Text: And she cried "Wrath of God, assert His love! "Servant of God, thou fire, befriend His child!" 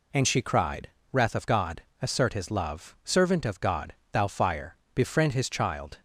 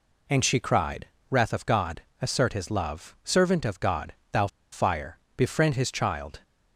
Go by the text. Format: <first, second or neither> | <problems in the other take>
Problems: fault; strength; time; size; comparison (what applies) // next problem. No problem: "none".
first | pauses between "cried" and "Wrath"; slight; at 1.0 s; 0.24 s long; slight in the first // pauses between "thou" and "fire"; slight; at 4.4 s; 0.24 s long